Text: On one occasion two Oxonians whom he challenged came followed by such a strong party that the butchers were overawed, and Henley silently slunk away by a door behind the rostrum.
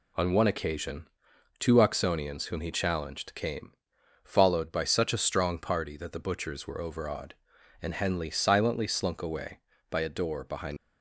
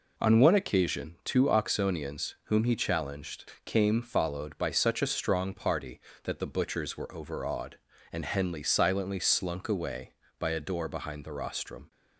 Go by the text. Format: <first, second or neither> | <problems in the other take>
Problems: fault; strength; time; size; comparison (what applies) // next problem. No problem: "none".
second | pauses between "occasion" and "two"; noticeable; at 1.0 s; 0.52 s long // pauses between "came" and "followed"; noticeable; at 3.7 s; 0.50 s long // stops before "the rostrum"; at 10.7 s